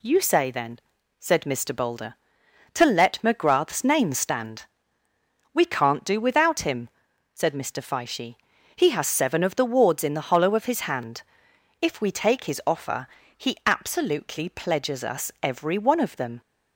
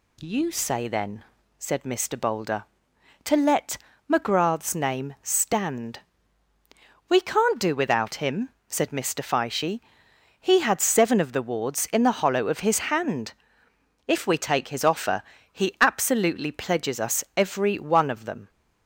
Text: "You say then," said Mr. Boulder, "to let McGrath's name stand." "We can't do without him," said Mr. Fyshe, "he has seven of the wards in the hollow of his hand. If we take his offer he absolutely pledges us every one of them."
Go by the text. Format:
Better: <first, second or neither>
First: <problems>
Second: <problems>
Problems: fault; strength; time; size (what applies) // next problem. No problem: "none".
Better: first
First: pauses between "offer" and "he"; slight; at 13.0 s; 0.28 s long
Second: pauses between "let" and "McGrath's"; slight; at 3.7 s; 0.34 s long // says "had" for "has"; at 10.5 s // pauses between "offer" and "he"; slight; at 15.2 s; 0.30 s long